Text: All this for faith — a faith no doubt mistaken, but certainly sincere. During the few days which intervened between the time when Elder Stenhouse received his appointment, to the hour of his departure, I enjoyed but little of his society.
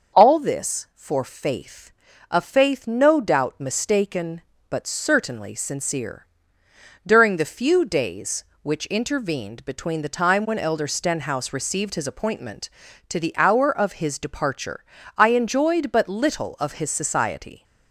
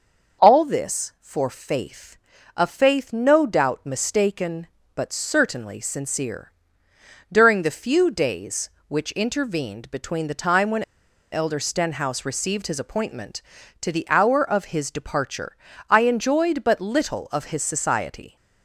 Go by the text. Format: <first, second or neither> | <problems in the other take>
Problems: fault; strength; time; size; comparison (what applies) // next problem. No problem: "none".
first | starts louder than the rest; until 1.5 s; 6 dB; also in the first // pauses between "when" and "Elder"; noticeable; at 10.8 s; 0.50 s long